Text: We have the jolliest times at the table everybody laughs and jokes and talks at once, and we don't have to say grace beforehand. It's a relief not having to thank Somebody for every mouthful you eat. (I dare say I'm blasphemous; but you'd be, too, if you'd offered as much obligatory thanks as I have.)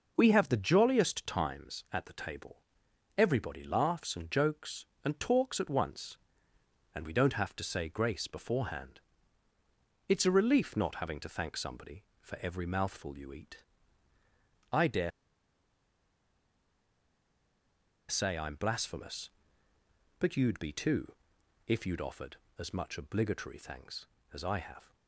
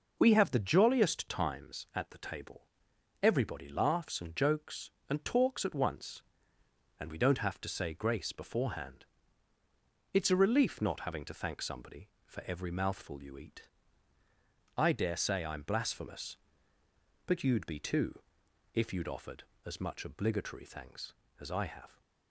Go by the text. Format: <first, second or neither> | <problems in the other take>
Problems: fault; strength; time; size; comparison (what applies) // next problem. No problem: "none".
second | pauses between "table" and "everybody"; noticeable; at 2.6 s; 0.56 s long; noticeable in the second // pauses between "dare" and "say"; strong; at 15.1 s; 2.9 s long